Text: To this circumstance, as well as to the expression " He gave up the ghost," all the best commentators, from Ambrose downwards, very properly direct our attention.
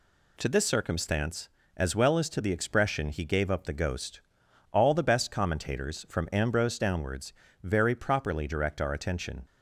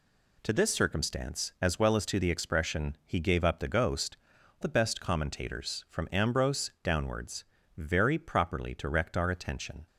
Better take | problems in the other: first | skips "all"; at 4.3 s

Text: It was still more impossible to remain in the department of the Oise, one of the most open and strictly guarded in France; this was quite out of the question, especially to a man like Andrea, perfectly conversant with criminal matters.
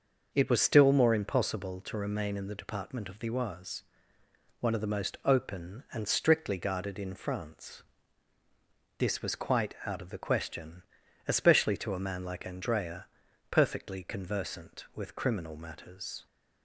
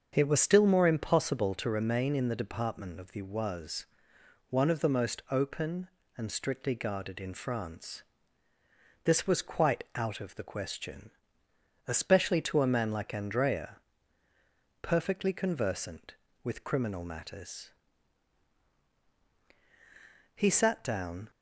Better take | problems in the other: first | starts louder than the rest; until 1.1 s; 6.5 dB // goes on to say "He sat down"; noticeable; from 20.3 s on; 0.94 s long

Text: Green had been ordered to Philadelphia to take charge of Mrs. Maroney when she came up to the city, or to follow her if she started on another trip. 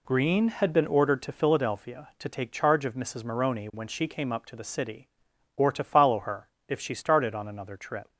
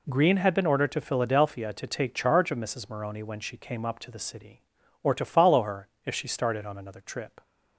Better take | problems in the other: neither | pauses between "her" and "if"; slight; the same in both

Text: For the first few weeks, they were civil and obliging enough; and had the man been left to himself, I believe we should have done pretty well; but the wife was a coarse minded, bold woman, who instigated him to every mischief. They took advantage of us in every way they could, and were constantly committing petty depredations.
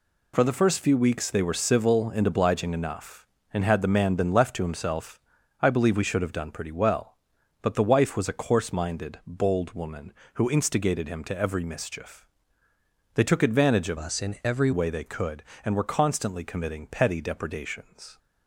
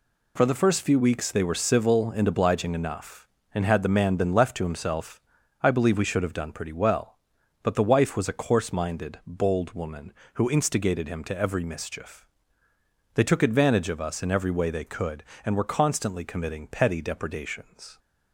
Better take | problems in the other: second | changes voice from "us" to "every"; from 13.9 to 14.7 s; 0.8 s long

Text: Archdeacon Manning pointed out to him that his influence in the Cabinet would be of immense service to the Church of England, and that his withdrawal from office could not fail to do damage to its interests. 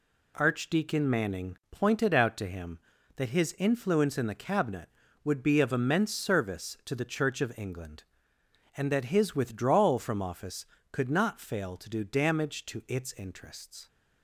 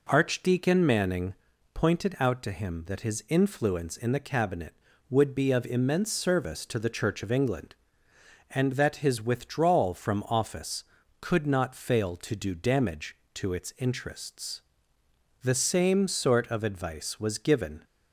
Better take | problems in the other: first | pauses between "Manning" and "pointed"; at 1.3 s; 0.40 s long // goes on to say "The same sort of advice was given"; strong; from 15.4 s on; 2.4 s long

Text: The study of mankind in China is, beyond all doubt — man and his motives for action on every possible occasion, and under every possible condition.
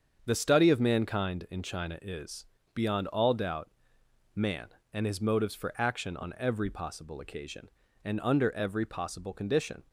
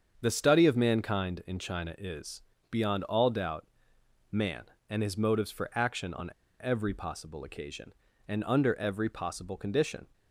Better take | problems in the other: first | starts louder than the rest; until 1.2 s; 7 dB; also in the first // pauses between "on" and "every"; slight; at 6.3 s; 0.30 s long

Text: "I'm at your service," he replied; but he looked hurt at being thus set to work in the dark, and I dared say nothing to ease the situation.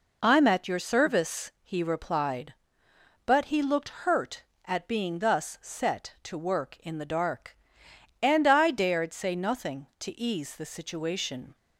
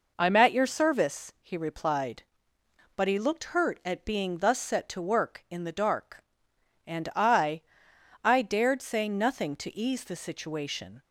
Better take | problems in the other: first | says "I" twice; at 8.2 s

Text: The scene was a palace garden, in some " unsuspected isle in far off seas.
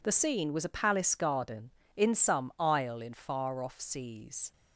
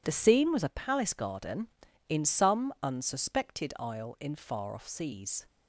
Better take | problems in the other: second | skips "unsuspected"; at 2.5 s

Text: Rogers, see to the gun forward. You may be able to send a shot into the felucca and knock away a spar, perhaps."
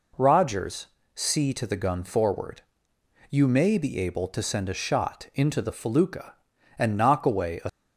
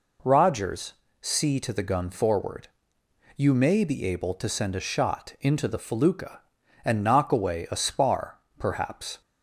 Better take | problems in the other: second | stops before "spar perhaps"; at 7.6 s

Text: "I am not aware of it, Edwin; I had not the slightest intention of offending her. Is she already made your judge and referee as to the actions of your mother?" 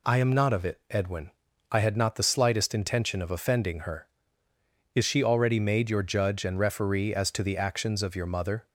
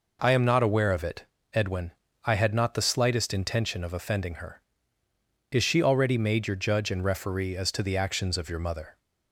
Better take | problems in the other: second | skips "aware"; at 0.5 s

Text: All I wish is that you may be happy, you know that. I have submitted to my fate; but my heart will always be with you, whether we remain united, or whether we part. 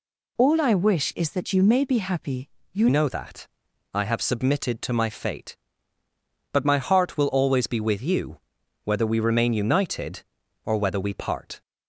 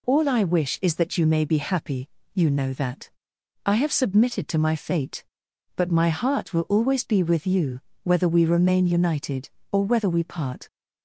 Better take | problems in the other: second | changes voice at "know"; from 2.8 s on; 8.8 s long

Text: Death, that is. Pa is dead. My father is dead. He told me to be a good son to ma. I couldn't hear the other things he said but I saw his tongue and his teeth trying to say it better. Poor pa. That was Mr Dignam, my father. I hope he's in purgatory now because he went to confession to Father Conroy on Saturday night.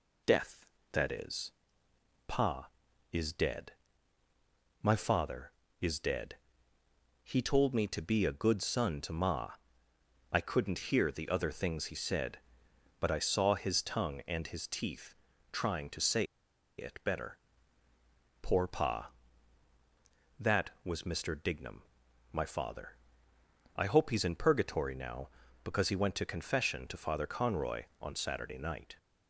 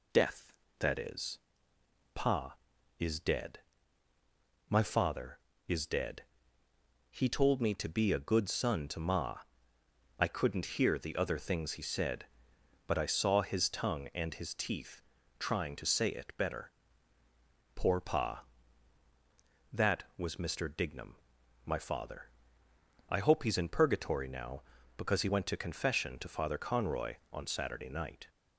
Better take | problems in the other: second | pauses between "teeth" and "trying"; at 15.1 s; 0.38 s long; also in the second // pauses between "say" and "it"; noticeable; at 16.2 s; 0.54 s long

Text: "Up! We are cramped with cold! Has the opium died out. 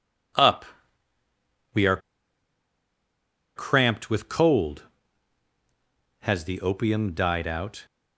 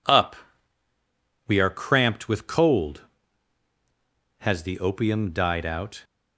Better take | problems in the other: second | pauses between "are" and "cramped"; strong; at 1.9 s; 1.5 s long

